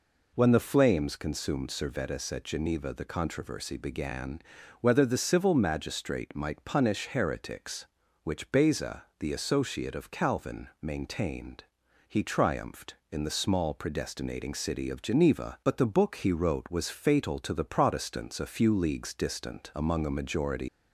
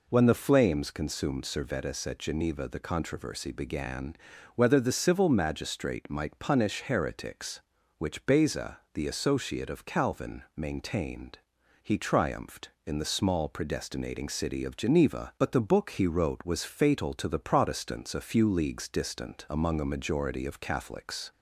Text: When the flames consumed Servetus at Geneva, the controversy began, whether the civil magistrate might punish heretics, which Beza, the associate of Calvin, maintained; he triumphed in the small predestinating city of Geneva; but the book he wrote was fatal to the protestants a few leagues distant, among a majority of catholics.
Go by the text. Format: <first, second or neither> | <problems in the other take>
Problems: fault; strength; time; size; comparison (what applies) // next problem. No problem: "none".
second | stops before "of catholics"; at 20.6 s